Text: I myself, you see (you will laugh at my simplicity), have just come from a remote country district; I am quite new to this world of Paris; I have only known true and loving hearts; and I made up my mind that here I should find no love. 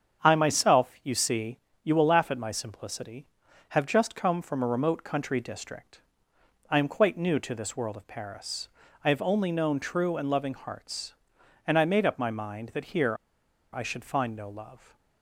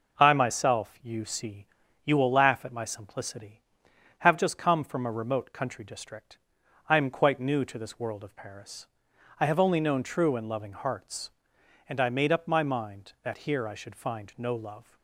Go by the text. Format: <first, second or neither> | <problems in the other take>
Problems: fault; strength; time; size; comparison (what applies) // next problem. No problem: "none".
second | starts louder than the rest; strong; until 1.3 s; 7.5 dB // pauses between "here" and "I"; noticeable; at 13.1 s; 0.57 s long